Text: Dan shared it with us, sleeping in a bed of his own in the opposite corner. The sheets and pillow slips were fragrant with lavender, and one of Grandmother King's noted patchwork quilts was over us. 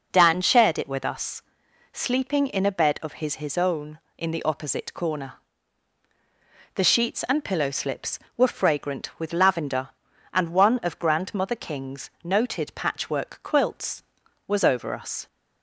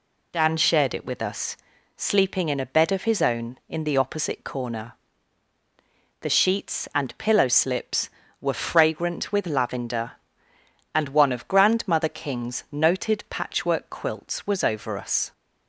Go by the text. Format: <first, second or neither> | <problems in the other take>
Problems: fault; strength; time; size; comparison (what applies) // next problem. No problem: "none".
second | says "his" twice; at 3.3 s